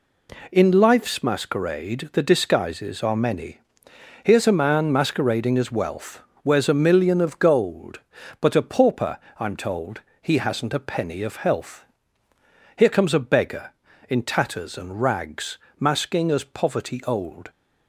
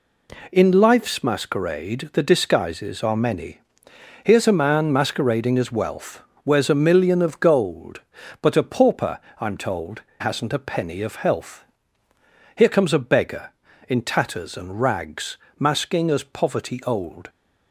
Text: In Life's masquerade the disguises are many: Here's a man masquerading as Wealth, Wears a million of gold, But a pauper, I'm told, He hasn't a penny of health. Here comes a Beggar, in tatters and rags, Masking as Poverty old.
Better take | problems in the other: first | skips "He"; at 10.1 s

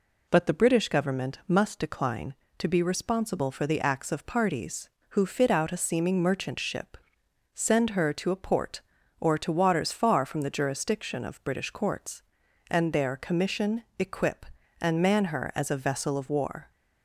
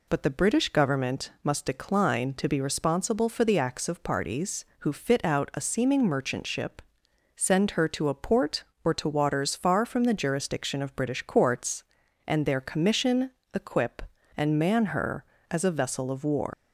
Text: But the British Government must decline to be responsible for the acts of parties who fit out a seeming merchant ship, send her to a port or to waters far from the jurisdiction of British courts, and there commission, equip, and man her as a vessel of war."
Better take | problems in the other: first | leaves "war" unfinished; at 16.5 s; 145 ms

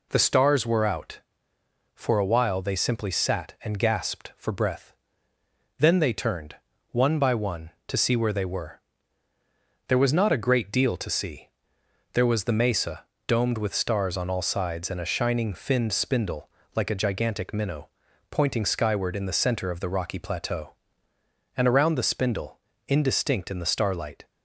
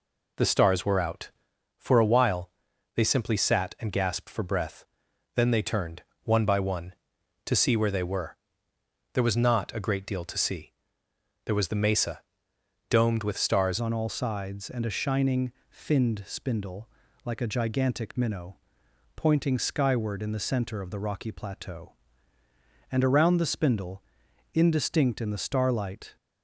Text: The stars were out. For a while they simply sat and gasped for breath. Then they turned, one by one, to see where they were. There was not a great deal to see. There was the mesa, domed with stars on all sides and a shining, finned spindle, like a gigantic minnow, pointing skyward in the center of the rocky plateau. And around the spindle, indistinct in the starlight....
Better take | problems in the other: first | pauses between "while" and "they"; noticeable; at 2.4 s; 0.46 s long // changes voice at "on"; from 13.7 s on; 12.4 s long

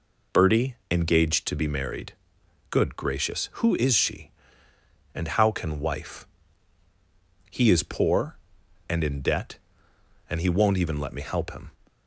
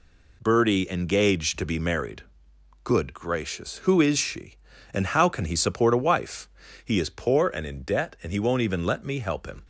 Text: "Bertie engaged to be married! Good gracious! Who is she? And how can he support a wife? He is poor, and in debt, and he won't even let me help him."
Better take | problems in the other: second | pauses between "Bertie" and "engaged"; slight; at 0.7 s; 0.16 s long // skips "he support a"; at 5.7 s

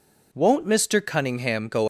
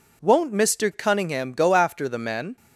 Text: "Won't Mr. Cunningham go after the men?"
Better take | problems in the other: second | stops before "after the men"; at 1.8 s

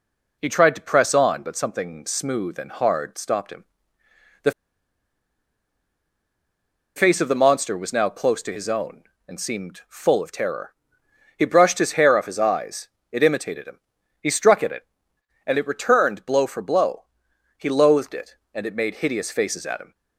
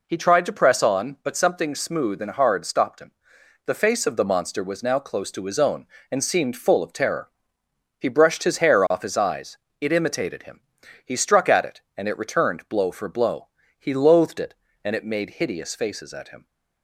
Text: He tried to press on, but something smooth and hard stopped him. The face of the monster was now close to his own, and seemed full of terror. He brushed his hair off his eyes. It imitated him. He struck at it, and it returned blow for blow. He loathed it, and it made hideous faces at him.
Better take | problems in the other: second | pauses between "The" and "face"; strong; at 4.5 s; 2.4 s long

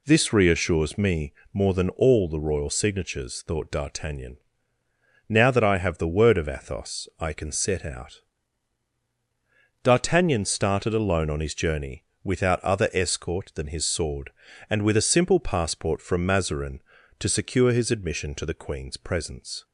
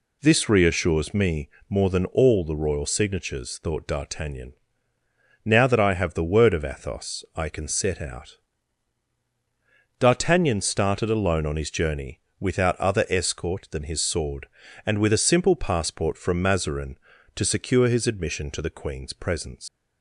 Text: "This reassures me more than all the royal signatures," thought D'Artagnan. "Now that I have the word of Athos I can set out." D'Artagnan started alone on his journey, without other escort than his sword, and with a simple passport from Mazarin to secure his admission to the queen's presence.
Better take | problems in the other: first | pauses between "me" and "more"; slight; at 1.4 s; 0.20 s long; slight in the first // leaves "presence" unfinished; at 19.6 s; 135 ms

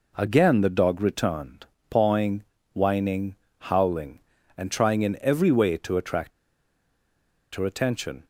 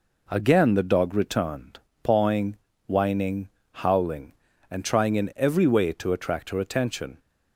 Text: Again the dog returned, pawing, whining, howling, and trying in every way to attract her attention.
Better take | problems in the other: second | pauses between "attract" and "her"; at 6.3 s; 1.2 s long

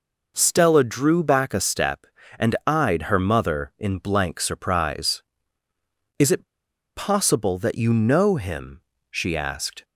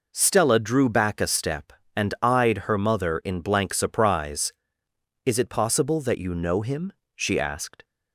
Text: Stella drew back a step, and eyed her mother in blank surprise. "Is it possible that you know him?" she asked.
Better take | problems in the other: second | pauses between "it" and "possible"; noticeable; at 6.4 s; 0.51 s long

